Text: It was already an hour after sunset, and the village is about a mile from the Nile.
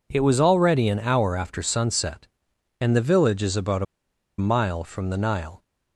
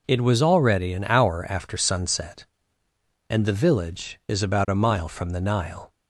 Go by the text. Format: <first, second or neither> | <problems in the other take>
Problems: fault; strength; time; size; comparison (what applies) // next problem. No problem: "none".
second | pauses between "a" and "mile"; noticeable; at 3.8 s; 0.54 s long